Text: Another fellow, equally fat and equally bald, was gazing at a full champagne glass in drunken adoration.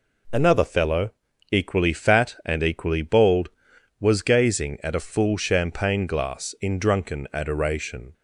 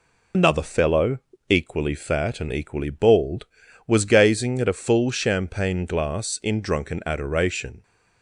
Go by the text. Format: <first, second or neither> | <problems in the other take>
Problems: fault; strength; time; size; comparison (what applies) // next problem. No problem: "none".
first | loses the start of "Another"; at 0.3 s; 65 ms